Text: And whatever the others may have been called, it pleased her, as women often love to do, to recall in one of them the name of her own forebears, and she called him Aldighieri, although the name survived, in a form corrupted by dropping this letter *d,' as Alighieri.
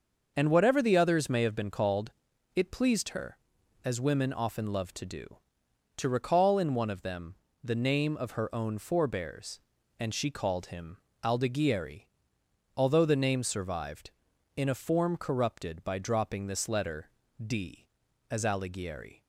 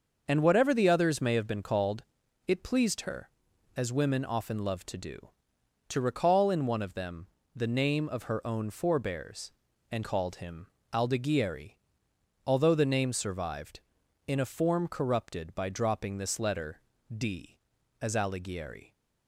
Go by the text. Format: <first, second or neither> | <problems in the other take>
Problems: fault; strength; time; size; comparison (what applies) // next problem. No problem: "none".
first | starts louder than the rest; until 1.2 s; 6 dB; also in the first // pauses between "them" and "the"; slight; at 7.2 s; 0.30 s long; slight in the first // skips "she"; at 10.0 s // pauses between "him" and "Aldighieri"; slight; at 10.6 s; 0.26 s long; slight in the first // pauses between "letter" and "d"; slight; at 16.7 s; 0.36 s long; slight in the first